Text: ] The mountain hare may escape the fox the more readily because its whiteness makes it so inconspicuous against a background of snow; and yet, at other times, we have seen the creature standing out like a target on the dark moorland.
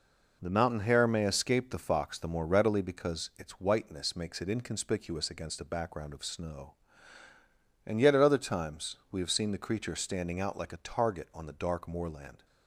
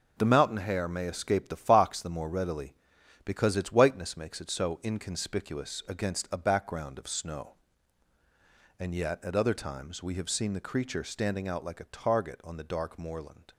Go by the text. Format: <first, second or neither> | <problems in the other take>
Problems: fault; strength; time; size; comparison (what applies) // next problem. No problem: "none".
second | skips "so"; at 4.4 s